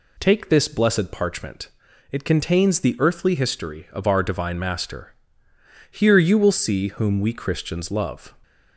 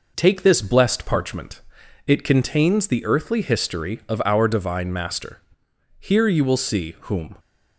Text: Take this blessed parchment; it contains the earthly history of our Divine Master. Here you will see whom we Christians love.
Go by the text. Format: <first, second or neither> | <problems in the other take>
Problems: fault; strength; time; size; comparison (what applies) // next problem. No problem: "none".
first | stops before "we Christians love"; at 7.3 s